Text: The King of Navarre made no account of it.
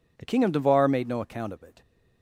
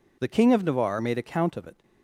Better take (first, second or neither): first